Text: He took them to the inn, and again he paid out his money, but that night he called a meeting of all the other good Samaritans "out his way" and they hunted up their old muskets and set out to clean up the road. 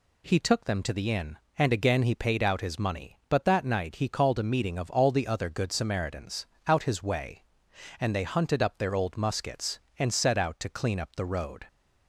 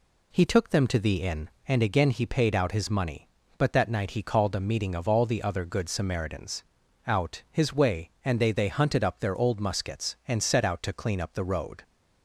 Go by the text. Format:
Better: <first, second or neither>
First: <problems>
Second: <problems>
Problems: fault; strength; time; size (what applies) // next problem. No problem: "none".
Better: first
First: pauses between "Samaritans" and "out"; slight; at 6.4 s; 0.18 s long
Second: pauses between "Samaritans" and "out"; at 6.6 s; 0.42 s long // says "they" twice; at 8.5 s